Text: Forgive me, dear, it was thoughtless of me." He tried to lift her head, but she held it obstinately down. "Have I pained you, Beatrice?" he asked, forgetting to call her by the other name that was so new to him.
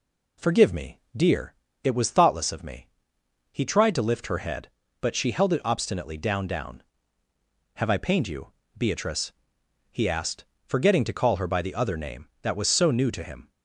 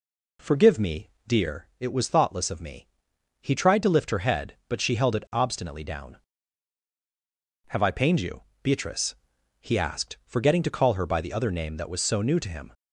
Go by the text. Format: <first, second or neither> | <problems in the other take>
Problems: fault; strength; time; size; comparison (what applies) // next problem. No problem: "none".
second | says "down" twice; at 6.4 s